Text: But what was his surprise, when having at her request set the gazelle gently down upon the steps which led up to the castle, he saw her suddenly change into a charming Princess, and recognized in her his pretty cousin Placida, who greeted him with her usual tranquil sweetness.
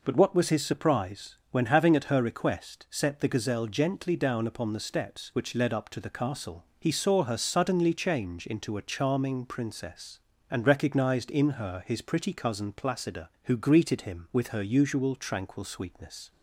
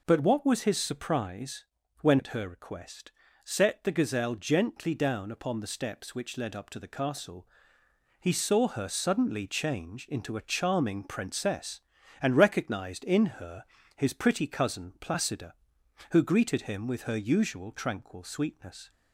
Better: first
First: none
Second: skips "having"; at 2.1 s // pauses between "request" and "set"; slight; at 3.1 s; 0.32 s long // pauses between "her" and "his"; slight; at 13.6 s; 0.34 s long

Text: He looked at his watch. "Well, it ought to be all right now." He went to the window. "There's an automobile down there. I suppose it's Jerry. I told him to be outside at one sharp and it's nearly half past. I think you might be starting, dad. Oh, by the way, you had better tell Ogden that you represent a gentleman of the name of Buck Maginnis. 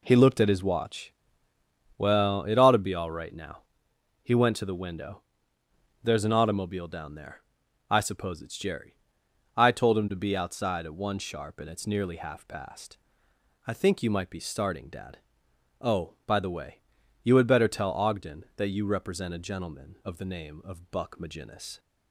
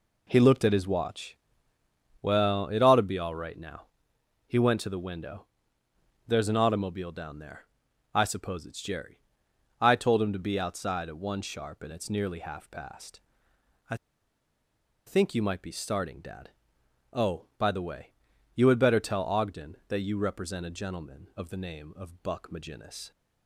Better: first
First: none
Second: pauses between "I" and "think"; at 13.9 s; 1.1 s long

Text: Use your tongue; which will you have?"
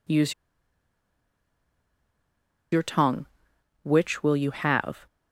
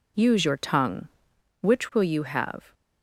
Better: second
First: pauses between "Use" and "your"; strong; at 0.3 s; 2.4 s long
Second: none

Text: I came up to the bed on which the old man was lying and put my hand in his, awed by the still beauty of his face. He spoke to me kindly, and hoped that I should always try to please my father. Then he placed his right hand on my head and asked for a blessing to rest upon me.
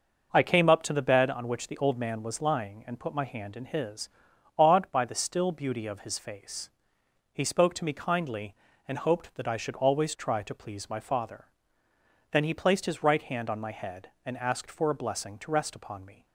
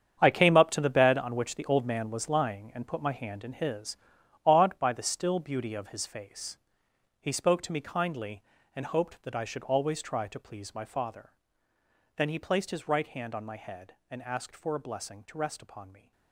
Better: first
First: starts louder than the rest; noticeable; until 1.3 s; 6 dB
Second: gets quieter; strong; throughout; 12.5 dB // starts louder than the rest; strong; until 1.2 s; 8.5 dB

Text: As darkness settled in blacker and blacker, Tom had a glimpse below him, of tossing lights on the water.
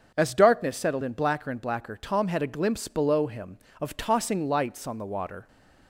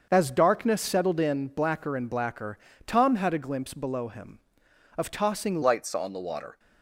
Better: first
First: starts louder than the rest; until 1.1 s; 7 dB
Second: starts louder than the rest; until 1.1 s; 6.5 dB // changes voice at "lights"; from 5.6 s on; 0.9 s long

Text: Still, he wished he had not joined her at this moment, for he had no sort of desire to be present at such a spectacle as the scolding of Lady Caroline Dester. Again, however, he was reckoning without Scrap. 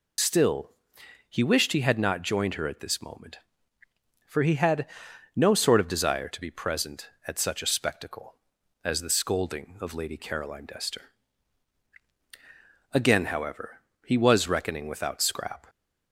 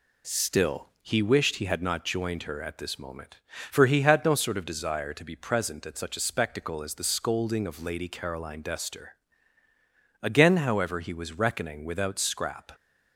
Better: second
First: loses the start of "Still"; at 0.1 s; 70 ms // pauses between "had" and "no"; noticeable; at 4.8 s; 0.50 s long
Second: none

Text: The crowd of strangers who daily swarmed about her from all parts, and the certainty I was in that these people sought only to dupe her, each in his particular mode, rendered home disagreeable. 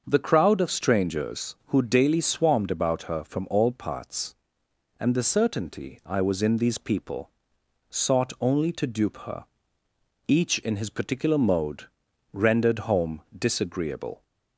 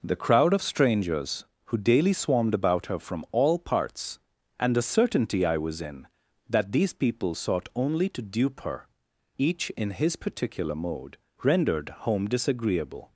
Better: second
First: starts louder than the rest; until 1.0 s; 6.5 dB // skips "that"; at 6.5 s // pauses between "people" and "sought"; noticeable; at 7.2 s; 0.58 s long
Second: none

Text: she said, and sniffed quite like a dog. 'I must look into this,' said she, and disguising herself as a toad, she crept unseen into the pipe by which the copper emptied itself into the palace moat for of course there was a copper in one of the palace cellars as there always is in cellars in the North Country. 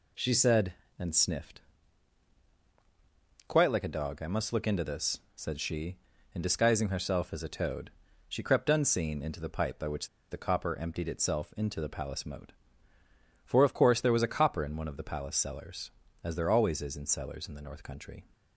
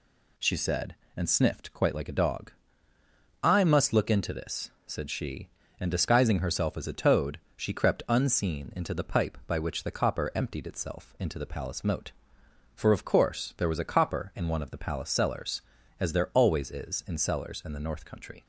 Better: second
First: pauses between "sniffed" and "quite"; strong; at 1.5 s; 1.8 s long // pauses between "which" and "the"; slight; at 10.0 s; 0.22 s long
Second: none

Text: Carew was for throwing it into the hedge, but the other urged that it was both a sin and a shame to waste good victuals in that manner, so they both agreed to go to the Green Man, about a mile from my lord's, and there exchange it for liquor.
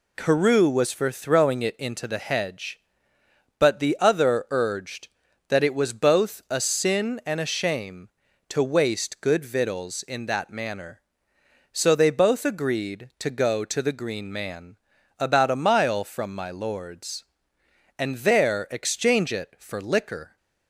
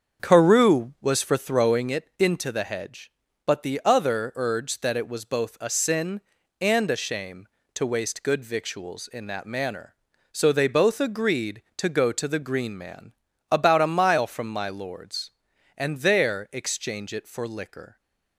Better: first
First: none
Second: starts louder than the rest; until 2.0 s; 7 dB

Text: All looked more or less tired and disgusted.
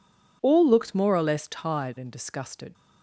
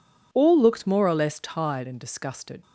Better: neither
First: none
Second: none

